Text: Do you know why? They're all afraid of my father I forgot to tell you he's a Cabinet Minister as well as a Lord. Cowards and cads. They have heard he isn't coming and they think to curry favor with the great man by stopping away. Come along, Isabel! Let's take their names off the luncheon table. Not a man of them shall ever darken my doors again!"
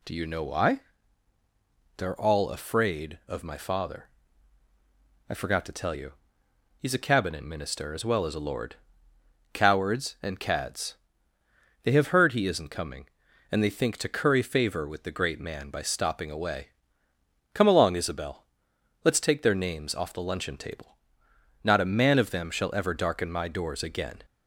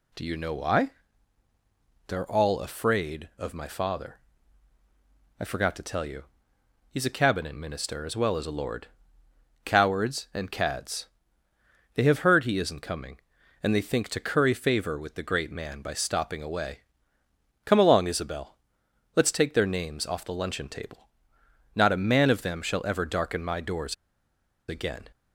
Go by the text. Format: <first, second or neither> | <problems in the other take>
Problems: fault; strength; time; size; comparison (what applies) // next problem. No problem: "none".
first | pauses between "father" and "I"; at 4.1 s; 1.2 s long; also in the first // pauses between "you" and "he's"; noticeable; at 6.2 s; 0.66 s long; noticeable in the first // pauses between "doors" and "again"; noticeable; at 23.9 s; 0.74 s long